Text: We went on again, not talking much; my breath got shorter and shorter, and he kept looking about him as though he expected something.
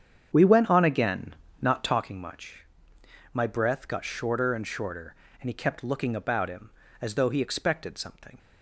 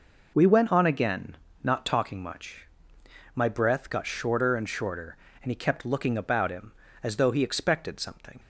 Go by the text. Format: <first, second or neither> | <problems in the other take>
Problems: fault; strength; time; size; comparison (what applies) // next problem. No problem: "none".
second | starts louder than the rest; strong; until 2.1 s; 8 dB